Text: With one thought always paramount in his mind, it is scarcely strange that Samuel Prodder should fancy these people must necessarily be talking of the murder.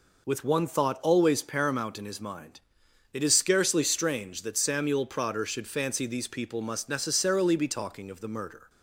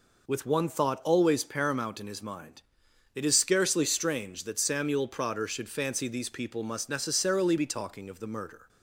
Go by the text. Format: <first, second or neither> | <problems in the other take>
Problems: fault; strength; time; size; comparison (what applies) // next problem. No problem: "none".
neither | none